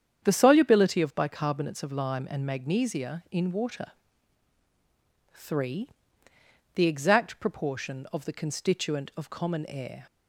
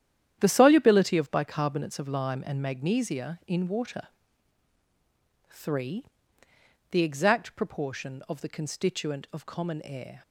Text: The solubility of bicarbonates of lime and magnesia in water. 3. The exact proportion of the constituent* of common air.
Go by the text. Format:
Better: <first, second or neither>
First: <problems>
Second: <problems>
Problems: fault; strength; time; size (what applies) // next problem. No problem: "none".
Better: first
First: starts louder than the rest; strong; until 1.2 s; 8.5 dB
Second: gets quieter; strong; throughout; 10 dB // starts louder than the rest; strong; until 1.4 s; 10 dB